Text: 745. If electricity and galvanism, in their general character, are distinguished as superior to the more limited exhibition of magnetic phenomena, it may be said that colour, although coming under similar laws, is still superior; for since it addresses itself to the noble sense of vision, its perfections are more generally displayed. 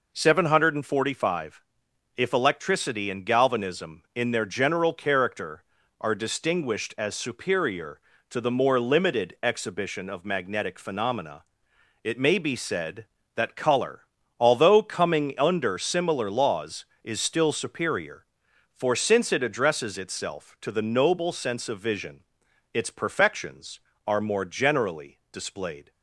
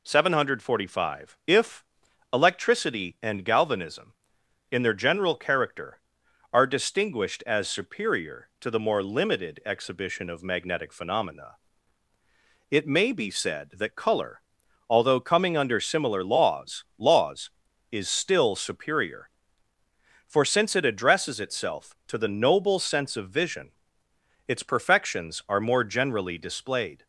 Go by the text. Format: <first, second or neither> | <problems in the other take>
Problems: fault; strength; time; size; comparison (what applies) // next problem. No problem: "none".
first | pauses between "If" and "electricity"; noticeable; at 1.8 s; 0.48 s long // says "laws" twice; at 16.9 s